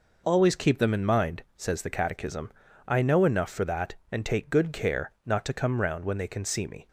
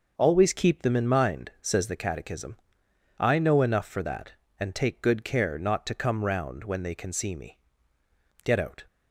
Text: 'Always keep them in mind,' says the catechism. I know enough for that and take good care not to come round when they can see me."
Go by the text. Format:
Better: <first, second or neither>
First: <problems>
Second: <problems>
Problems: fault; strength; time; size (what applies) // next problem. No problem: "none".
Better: first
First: none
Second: goes on to say "Get out"; slight; from 8.4 s on; 0.42 s long